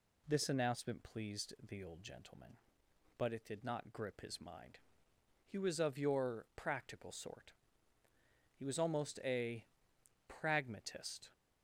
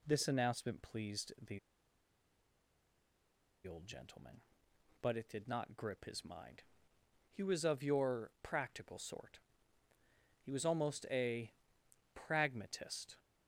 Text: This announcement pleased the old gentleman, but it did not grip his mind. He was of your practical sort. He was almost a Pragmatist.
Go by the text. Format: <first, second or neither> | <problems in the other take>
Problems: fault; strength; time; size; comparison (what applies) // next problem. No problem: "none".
first | pauses between "the" and "old"; strong; at 1.5 s; 2.0 s long // pauses between "a" and "Pragmatist"; noticeable; at 11.5 s; 0.64 s long; noticeable in the first